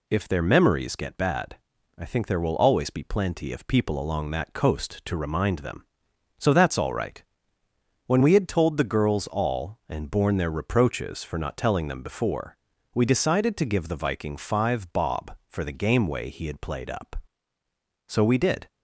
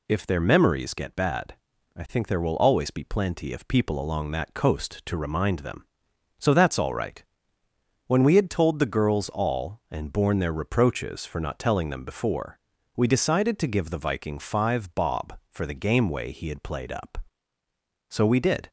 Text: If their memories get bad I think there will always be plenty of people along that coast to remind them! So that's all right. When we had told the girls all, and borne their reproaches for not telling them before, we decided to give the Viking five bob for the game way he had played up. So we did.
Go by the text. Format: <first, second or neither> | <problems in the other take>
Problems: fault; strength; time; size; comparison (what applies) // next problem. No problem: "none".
neither | pauses between "bad" and "I"; the same in both